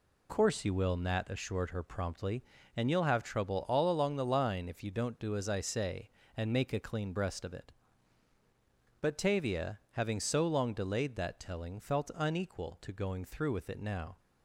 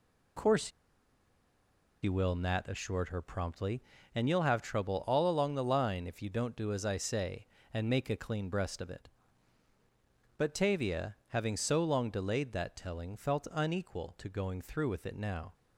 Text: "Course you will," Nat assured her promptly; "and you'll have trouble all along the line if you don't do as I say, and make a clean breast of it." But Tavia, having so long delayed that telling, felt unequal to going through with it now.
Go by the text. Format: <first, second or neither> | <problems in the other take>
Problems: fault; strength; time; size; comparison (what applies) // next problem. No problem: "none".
first | pauses between "Course" and "you"; strong; at 0.6 s; 1.3 s long